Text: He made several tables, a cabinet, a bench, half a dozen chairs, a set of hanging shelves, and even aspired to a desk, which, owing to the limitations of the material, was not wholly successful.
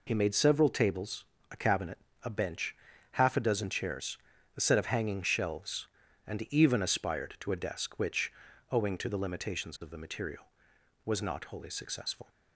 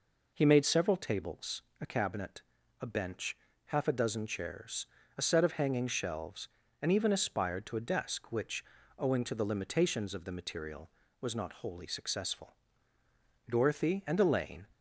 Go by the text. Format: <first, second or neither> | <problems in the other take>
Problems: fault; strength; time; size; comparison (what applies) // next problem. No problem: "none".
first | goes on to say "Dorothy and Elaine"; noticeable; from 13.4 s on; 1.1 s long